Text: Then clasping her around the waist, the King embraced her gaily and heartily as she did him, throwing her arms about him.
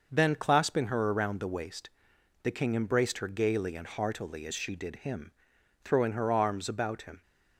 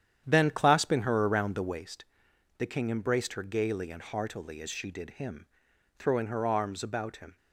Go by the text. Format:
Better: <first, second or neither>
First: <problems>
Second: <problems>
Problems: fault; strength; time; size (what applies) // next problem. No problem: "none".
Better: first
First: none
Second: starts louder than the rest; strong; until 1.8 s; 9.5 dB